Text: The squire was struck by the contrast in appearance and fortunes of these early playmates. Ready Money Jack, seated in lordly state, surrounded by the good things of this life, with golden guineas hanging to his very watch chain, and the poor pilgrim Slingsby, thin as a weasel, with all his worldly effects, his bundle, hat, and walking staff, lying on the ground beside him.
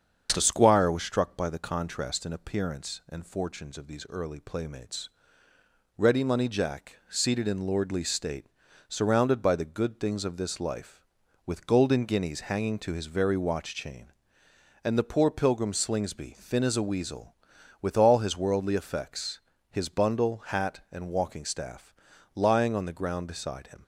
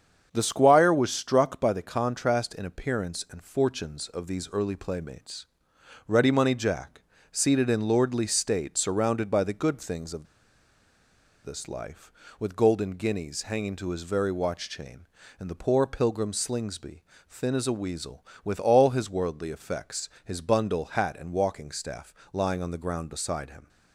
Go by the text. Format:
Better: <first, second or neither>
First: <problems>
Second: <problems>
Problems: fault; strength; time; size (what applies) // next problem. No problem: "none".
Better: first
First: starts louder than the rest; until 1.3 s; 7 dB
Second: starts louder than the rest; strong; until 1.3 s; 7.5 dB // pauses between "of" and "this"; at 10.2 s; 1.1 s long